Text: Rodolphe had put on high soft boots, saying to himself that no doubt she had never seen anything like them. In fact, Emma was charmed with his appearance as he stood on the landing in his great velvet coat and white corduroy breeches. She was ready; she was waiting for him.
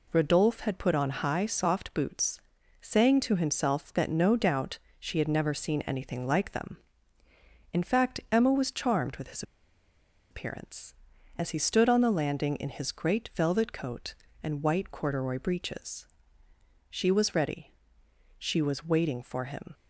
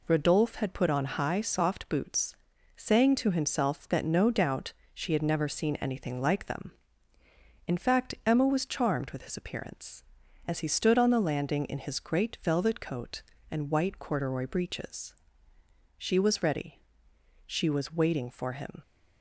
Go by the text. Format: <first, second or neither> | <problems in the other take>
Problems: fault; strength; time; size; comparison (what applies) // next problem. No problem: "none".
second | pauses between "doubt" and "she"; slight; at 4.7 s; 0.20 s long; slight in the second // pauses between "his" and "appearance"; noticeable; at 9.4 s; 0.88 s long